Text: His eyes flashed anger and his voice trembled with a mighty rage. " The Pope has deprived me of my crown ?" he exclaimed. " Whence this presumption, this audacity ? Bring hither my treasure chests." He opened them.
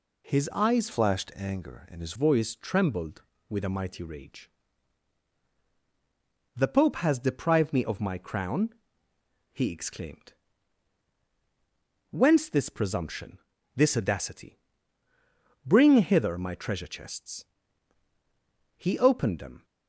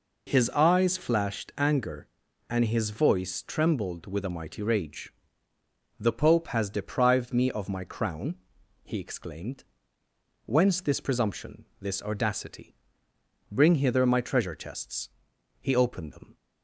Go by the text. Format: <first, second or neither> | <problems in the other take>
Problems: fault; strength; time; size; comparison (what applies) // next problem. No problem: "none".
second | changes voice from "flashed" to "his"; from 0.9 to 2.1 s; 1.2 s long